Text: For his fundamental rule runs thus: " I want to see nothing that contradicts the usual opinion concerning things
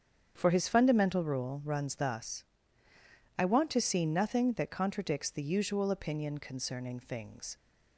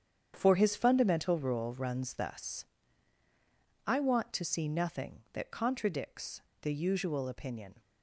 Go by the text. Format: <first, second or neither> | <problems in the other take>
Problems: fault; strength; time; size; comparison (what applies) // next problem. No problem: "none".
first | starts louder than the rest; strong; until 1.3 s; 7.5 dB; strong in the first // pauses between "contradicts" and "the"; slight; at 6.4 s; 0.19 s long // stops before "concerning things"; at 7.8 s